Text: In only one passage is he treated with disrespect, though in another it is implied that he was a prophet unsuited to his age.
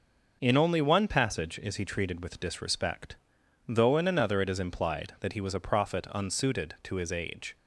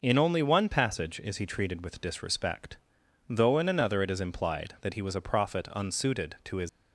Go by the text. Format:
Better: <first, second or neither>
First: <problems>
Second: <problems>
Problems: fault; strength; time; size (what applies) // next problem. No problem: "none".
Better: first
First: none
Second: stops before "age"; at 6.6 s